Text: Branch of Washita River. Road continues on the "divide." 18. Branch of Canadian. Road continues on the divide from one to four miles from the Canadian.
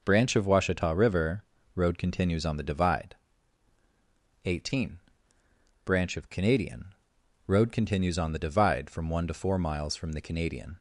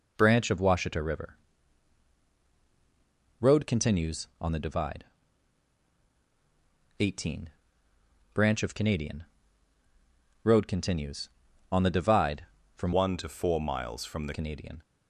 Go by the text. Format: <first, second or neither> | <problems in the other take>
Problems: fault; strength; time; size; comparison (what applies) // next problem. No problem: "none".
first | changes voice from "one" to "the"; from 12.9 to 14.3 s; 1.4 s long